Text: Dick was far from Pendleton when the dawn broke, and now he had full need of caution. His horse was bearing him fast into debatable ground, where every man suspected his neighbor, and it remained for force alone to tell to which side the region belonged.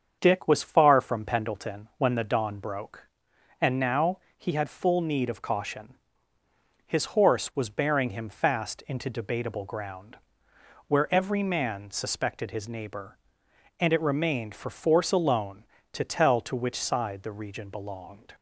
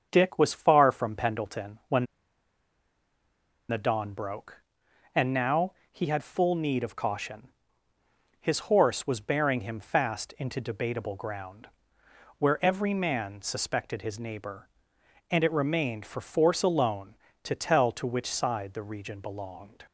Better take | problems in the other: first | starts louder than the rest; strong; until 1.1 s; 7 dB; strong in the first // pauses between "when" and "the"; strong; at 2.0 s; 1.6 s long // pauses between "now" and "he"; slight; at 5.7 s; 0.18 s long; slight in the first

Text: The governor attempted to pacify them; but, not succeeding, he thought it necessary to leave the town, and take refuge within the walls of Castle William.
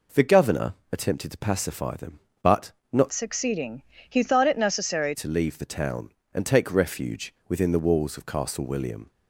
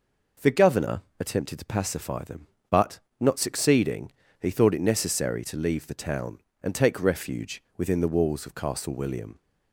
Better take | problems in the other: second | pauses between "governor" and "attempted"; slight; at 0.7 s; 0.16 s long; slight in the second // changes voice from "succeeding" to "necessary"; from 3.1 to 5.1 s; 2.0 s long

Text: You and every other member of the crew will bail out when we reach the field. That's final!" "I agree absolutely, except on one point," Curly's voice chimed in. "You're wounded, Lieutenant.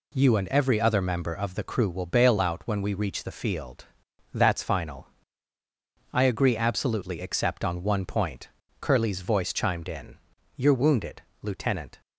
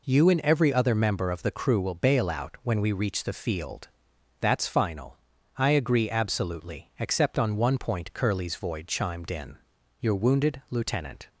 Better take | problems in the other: first | says "void" for "voice"; at 8.5 s

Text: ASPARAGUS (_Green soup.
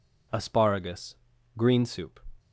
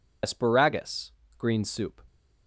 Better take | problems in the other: first | loses the start of "ASPARAGUS"; at 0.2 s; 60 ms

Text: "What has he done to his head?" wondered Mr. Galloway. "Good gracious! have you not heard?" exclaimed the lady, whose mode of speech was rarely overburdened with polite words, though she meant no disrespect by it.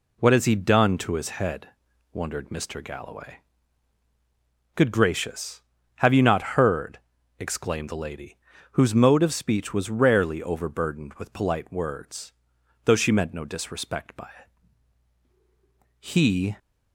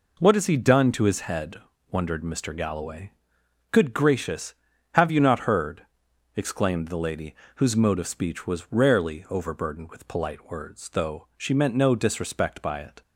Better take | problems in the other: second | goes on to say "He"; from 16.0 s on; 0.56 s long

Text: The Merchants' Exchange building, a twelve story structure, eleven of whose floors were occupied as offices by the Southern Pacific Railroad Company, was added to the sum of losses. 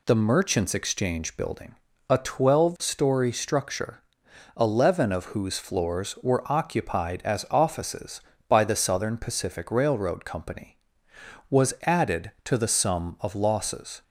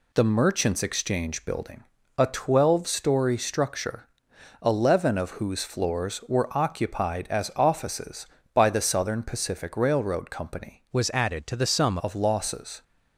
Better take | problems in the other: first | changes voice from "was" to "sum"; from 10.9 to 11.9 s; 1.0 s long

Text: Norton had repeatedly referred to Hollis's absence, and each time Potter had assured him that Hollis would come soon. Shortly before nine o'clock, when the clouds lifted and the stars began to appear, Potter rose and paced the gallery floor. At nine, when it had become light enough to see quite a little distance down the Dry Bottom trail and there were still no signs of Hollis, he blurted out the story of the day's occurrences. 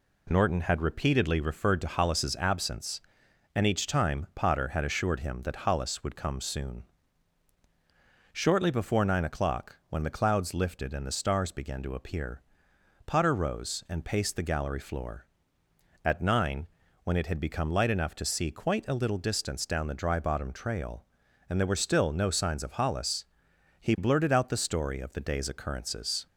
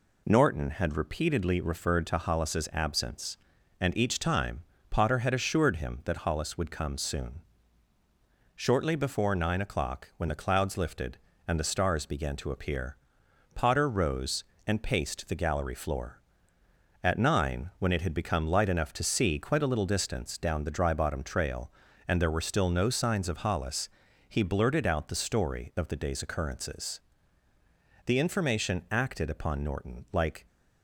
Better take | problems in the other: first | pauses between "time" and "Potter"; slight; at 4.6 s; 0.28 s long // goes on to say "The information acted upon Norton like"; strong; from 28.0 s on; 2.4 s long

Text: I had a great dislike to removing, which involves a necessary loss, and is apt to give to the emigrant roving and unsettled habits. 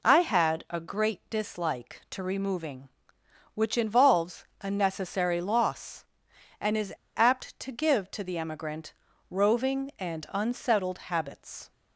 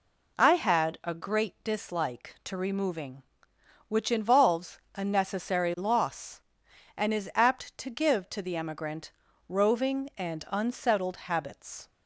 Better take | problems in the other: second | pauses between "is" and "apt"; slight; at 6.9 s; 0.20 s long // pauses between "emigrant" and "roving"; at 8.9 s; 0.40 s long; also in the second

